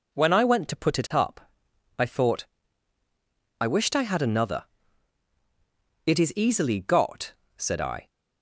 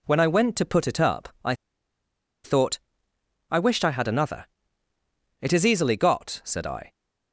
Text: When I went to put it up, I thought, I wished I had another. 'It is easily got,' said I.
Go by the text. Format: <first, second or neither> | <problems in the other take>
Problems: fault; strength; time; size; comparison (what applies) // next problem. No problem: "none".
first | pauses between "I" and "thought"; noticeable; at 1.5 s; 0.88 s long